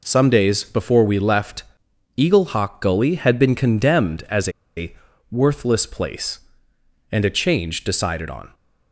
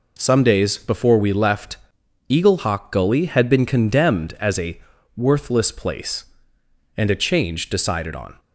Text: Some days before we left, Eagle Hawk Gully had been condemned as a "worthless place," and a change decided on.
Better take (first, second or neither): second